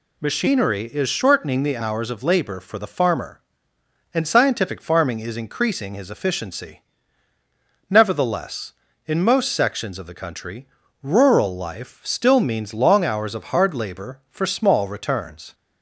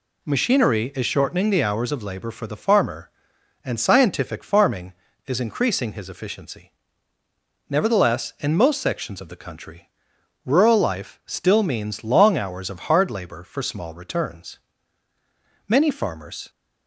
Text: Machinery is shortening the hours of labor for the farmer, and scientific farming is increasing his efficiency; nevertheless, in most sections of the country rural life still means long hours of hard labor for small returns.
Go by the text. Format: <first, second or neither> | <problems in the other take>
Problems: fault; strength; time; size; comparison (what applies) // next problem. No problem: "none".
first | pauses between "country" and "rural"; noticeable; at 9.8 s; 0.58 s long; also in the first // goes on to say "Many farmers"; noticeable; from 15.6 s on; 0.82 s long